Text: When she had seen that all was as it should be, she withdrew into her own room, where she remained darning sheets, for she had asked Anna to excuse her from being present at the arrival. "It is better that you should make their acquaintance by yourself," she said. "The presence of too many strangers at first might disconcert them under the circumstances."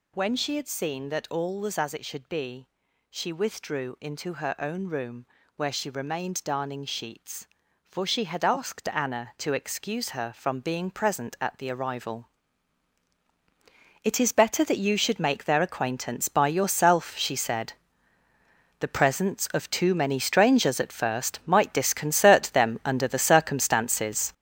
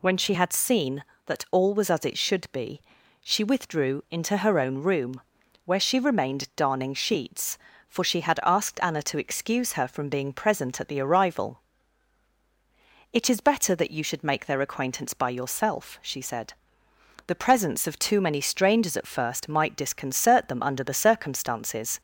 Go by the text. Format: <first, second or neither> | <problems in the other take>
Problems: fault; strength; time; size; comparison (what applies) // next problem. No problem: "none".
second | gets louder; strong; throughout; 9 dB